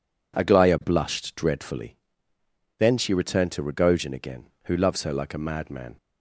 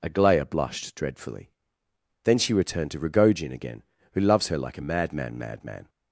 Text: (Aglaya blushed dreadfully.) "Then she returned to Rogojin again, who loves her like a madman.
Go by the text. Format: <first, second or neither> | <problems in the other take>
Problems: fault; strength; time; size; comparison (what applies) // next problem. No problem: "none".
first | says "madman" twice; at 5.3 s